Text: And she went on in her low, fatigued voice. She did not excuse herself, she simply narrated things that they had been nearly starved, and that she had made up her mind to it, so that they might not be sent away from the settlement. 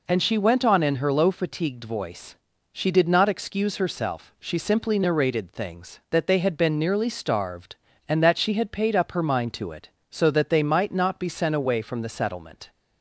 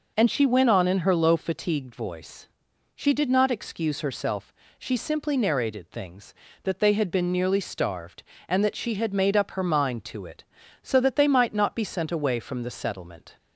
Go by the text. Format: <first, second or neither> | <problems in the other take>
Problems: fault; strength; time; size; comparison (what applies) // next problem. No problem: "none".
second | says "paid" for "made"; at 8.6 s